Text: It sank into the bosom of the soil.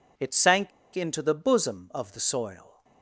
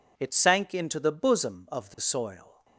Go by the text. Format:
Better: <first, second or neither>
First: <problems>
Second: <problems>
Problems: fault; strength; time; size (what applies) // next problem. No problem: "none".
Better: second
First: pauses between "sank" and "into"; slight; at 0.7 s; 0.25 s long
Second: none